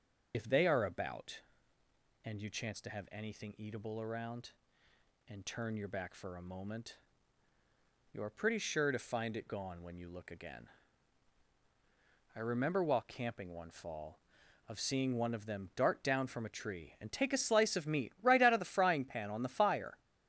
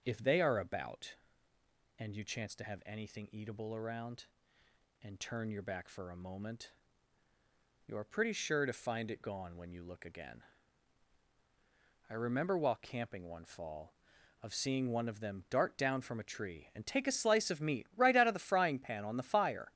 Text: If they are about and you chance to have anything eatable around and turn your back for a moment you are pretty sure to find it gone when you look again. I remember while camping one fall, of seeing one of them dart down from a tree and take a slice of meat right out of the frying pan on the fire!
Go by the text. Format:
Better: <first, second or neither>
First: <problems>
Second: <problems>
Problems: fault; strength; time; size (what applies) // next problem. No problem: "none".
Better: second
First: loses the start of "If"; at 0.3 s; 45 ms // starts louder than the rest; until 1.3 s; 6 dB // pauses between "moment" and "you"; at 6.9 s; 1.1 s long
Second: starts louder than the rest; until 1.0 s; 6.5 dB // pauses between "moment" and "you"; at 6.7 s; 1.1 s long